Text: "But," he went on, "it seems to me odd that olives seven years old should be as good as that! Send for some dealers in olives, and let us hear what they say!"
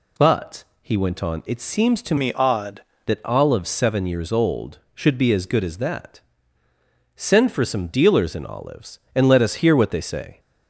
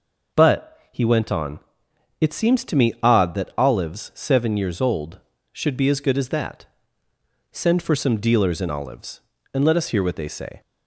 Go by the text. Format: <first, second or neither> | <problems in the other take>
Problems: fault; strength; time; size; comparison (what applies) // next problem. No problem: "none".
second | changes voice from "me" to "odd"; from 2.1 to 2.8 s; 0.7 s long